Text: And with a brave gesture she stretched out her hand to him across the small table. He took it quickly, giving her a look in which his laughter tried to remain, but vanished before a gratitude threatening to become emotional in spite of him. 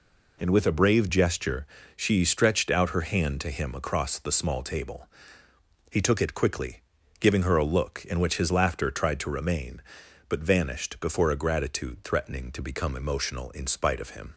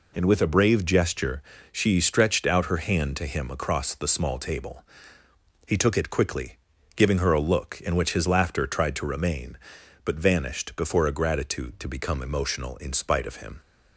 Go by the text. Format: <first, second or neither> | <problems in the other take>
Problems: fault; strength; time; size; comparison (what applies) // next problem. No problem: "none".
first | pauses between "gesture" and "she"; slight; at 1.4 s; 0.30 s long; slight in the first // skips "threatening"; at 11.7 s